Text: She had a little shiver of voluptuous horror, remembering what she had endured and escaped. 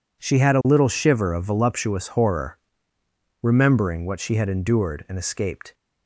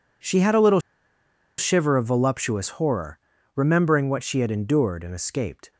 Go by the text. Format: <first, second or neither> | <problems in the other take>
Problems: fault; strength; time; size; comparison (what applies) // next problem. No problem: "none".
first | pauses between "little" and "shiver"; noticeable; at 0.7 s; 0.78 s long